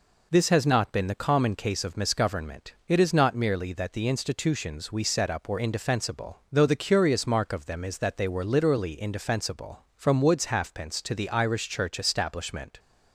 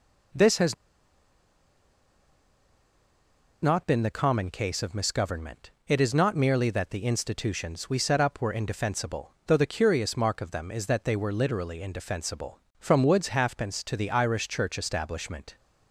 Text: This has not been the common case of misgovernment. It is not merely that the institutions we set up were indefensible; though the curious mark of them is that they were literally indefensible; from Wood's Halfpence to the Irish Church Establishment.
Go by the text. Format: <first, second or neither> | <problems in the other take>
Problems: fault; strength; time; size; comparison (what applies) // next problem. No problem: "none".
first | pauses between "has" and "not"; strong; at 0.7 s; 2.8 s long